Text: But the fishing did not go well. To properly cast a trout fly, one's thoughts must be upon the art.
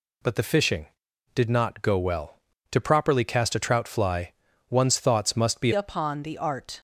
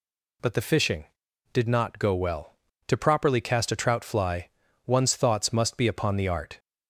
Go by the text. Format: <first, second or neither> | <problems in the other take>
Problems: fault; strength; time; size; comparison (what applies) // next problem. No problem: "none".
second | changes voice at "upon"; from 5.7 s on; 1.0 s long